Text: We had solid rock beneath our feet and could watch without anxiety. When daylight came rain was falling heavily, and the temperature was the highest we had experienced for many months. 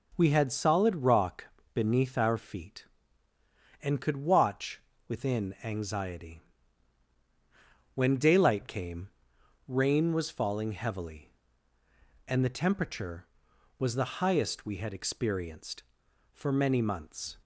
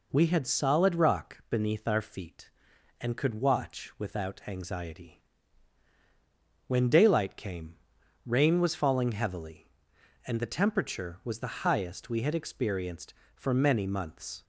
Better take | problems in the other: second | pauses between "rock" and "beneath"; slight; at 1.4 s; 0.26 s long // says "within" for "without"; at 5.0 s // pauses between "came" and "rain"; noticeable; at 9.0 s; 0.60 s long; noticeable in the second

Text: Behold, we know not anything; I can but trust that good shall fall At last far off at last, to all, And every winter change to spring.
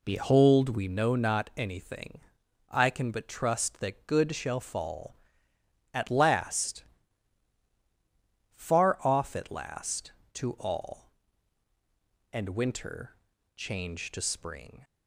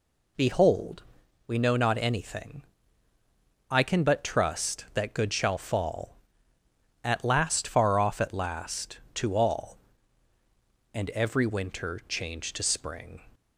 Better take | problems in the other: second | pauses between "last" and "far"; strong; at 6.8 s; 1.6 s long // skips "every"; at 12.4 s // pauses between "winter" and "change"; at 13.1 s; 0.40 s long

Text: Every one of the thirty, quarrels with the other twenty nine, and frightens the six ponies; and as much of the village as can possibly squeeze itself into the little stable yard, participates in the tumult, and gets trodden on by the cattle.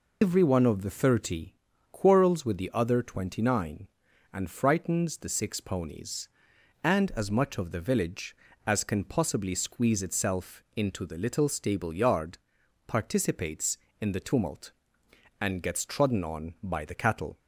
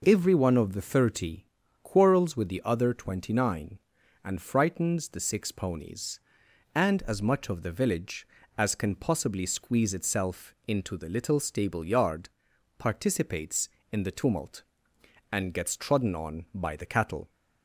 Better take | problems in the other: second | loses the start of "Every"; at 0.2 s; 105 ms

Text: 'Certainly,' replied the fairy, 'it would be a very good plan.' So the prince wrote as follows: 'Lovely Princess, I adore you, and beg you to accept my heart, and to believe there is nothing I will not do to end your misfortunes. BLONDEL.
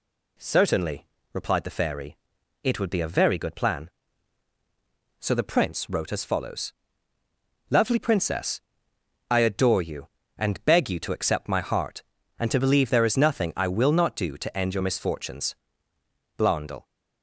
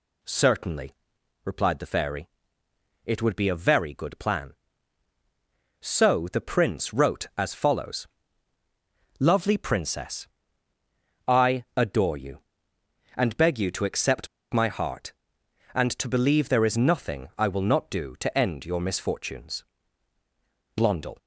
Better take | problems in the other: first | pauses between "accept" and "my"; slight; at 14.2 s; 0.25 s long

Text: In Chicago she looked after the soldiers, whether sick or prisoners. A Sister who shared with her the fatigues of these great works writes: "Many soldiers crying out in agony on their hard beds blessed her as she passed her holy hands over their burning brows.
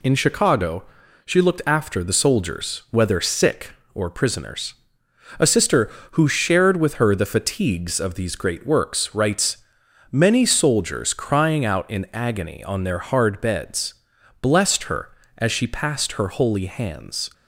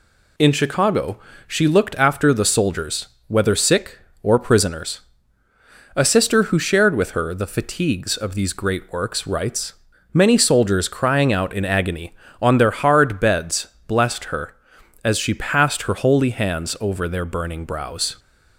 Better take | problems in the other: second | pauses between "Chicago" and "she"; at 0.8 s; 0.40 s long; slight in the second // pauses between "beds" and "blessed"; noticeable; at 13.9 s; 0.48 s long; slight in the second // stops before "over their burning brows"; at 17.3 s

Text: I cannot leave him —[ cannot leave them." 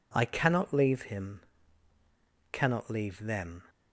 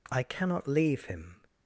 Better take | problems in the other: first | stops before "cannot leave them"; at 1.4 s

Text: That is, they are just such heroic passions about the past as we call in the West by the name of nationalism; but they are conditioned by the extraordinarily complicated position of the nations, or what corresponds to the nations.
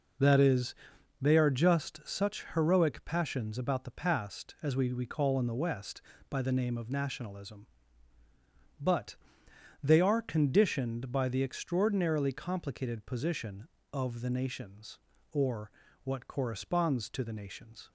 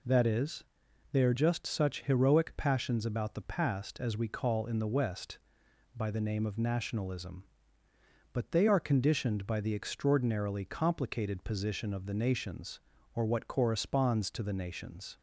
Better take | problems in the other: second | says "we" twice; at 4.9 s // pauses between "but" and "they"; noticeable; at 9.1 s; 0.68 s long // pauses between "or" and "what"; slight; at 15.7 s; 0.32 s long

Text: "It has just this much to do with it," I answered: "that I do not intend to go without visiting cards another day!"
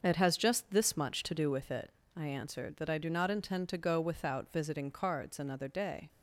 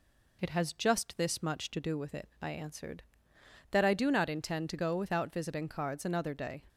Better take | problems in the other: second | starts louder than the rest; until 1.6 s; 6.5 dB

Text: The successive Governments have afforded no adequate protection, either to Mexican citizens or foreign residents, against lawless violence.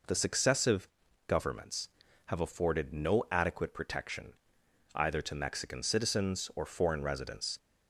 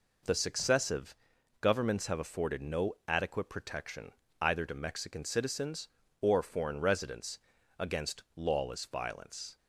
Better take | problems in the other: second | pauses between "successive" and "Governments"; at 0.8 s; 0.40 s long; noticeable in the second // stops before "against lawless violence"; at 7.5 s

